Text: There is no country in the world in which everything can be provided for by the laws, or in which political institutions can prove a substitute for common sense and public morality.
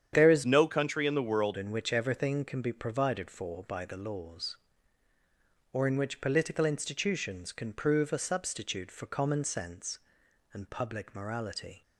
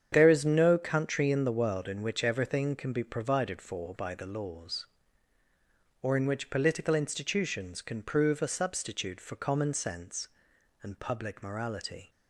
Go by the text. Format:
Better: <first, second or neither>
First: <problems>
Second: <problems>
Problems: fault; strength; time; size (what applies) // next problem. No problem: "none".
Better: second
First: starts louder than the rest; strong; until 1.1 s; 9 dB // changes voice from "no" to "world"; from 0.4 to 1.5 s; 1.1 s long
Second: starts louder than the rest; strong; until 1.1 s; 8.5 dB